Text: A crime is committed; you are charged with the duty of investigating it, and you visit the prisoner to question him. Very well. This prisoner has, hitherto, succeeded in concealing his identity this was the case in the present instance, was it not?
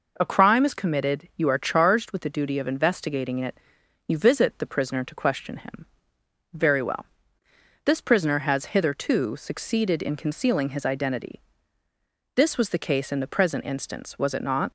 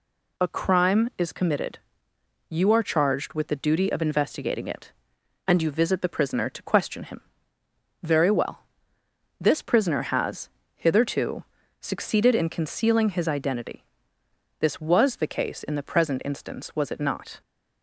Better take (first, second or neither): second